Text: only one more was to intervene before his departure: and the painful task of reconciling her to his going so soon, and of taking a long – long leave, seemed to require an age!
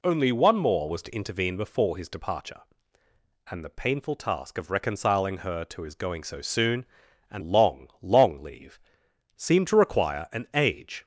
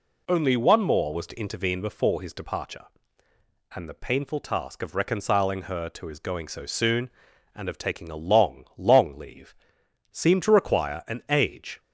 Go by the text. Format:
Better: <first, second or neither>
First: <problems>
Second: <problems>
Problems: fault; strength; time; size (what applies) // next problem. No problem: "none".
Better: second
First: skips "of taking a"; at 7.4 s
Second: none